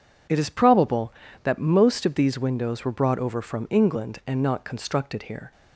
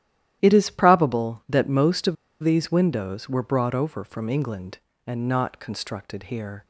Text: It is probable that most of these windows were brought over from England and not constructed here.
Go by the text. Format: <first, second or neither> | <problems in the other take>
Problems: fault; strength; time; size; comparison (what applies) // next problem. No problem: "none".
first | starts louder than the rest; strong; until 1.4 s; 12.5 dB // pauses between "of" and "these"; slight; at 2.1 s; 0.27 s long